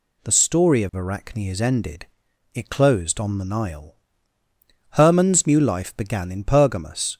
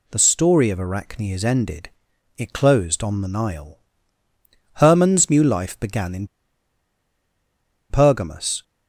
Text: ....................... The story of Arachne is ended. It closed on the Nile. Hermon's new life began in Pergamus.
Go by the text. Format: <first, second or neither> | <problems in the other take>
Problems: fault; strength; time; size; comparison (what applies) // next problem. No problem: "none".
first | pauses between "in" and "Pergamus"; strong; at 6.2 s; 1.6 s long